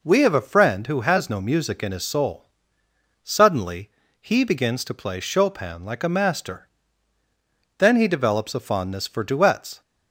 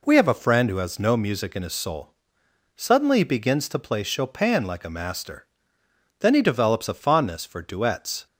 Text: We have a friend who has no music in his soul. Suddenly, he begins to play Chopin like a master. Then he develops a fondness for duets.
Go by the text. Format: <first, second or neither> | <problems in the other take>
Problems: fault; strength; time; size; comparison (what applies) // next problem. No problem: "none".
neither | none